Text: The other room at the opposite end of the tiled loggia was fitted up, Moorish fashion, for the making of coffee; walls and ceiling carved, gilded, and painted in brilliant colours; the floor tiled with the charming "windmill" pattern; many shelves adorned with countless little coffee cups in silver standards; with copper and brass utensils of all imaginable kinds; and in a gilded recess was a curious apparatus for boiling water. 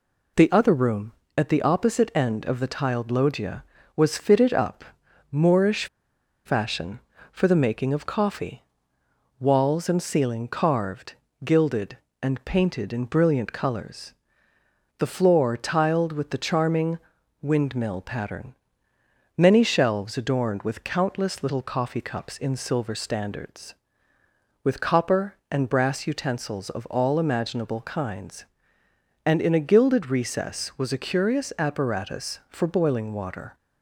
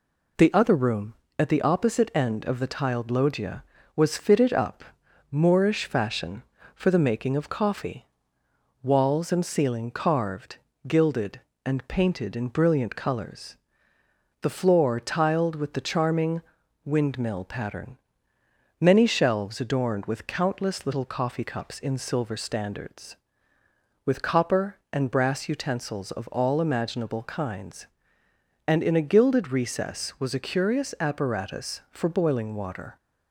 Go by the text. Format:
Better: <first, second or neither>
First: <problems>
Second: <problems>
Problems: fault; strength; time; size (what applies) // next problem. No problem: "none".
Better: second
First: pauses between "Moorish" and "fashion"; noticeable; at 5.8 s; 0.59 s long // pauses between "charming" and "windmill"; at 16.9 s; 0.42 s long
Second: pauses between "charming" and "windmill"; at 16.4 s; 0.42 s long